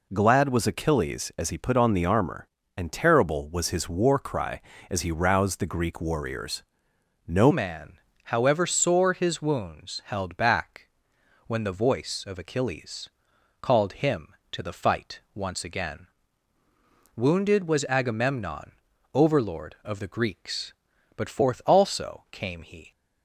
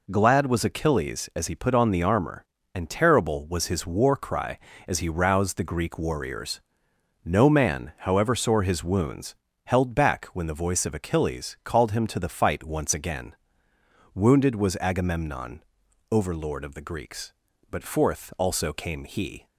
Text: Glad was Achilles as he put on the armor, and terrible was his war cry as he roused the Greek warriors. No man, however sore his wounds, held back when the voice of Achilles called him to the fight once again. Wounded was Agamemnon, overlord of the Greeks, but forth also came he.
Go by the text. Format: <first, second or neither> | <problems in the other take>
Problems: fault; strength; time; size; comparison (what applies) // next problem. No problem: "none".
second | changes voice at "man"; from 7.5 s on; 15.4 s long // pauses between "back" and "when"; noticeable; at 10.8 s; 0.60 s long // pauses between "Achilles" and "called"; noticeable; at 13.0 s; 0.52 s long // pauses between "fight" and "once"; slight; at 15.1 s; 0.16 s long